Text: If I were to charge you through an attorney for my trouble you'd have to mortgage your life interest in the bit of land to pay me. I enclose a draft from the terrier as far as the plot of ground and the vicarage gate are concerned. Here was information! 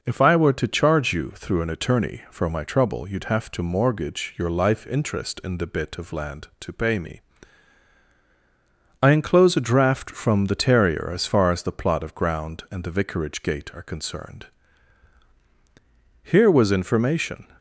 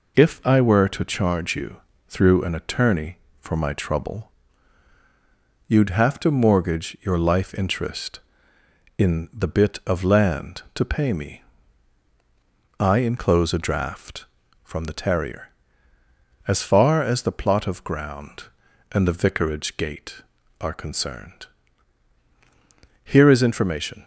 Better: first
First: none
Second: pauses between "you" and "through"; slight; at 1.7 s; 0.30 s long // pauses between "trouble" and "you'd"; strong; at 4.3 s; 1.3 s long // says "is" for "was"; at 23.3 s

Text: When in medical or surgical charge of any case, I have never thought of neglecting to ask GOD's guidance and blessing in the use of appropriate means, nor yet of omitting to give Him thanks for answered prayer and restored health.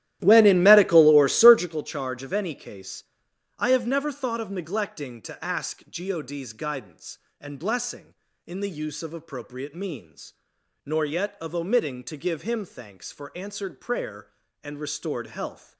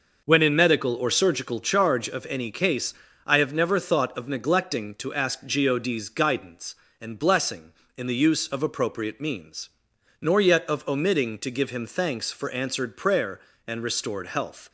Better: second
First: starts louder than the rest; strong; until 1.8 s; 13.5 dB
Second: none

